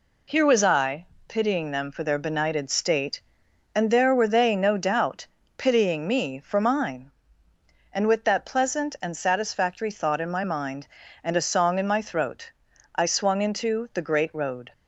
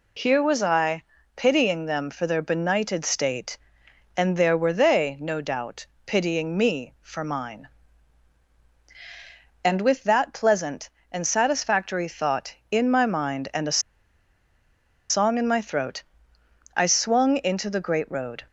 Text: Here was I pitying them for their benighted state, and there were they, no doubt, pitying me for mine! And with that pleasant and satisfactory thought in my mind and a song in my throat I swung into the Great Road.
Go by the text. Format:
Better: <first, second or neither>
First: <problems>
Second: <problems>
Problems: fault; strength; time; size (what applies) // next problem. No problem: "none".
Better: first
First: pauses between "I" and "pitying"; slight; at 1.0 s; 0.20 s long // pauses between "throat" and "I"; at 12.5 s; 0.42 s long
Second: pauses between "I" and "pitying"; slight; at 1.0 s; 0.32 s long // pauses between "a" and "song"; strong; at 13.8 s; 1.2 s long // pauses between "throat" and "I"; noticeable; at 16.0 s; 0.74 s long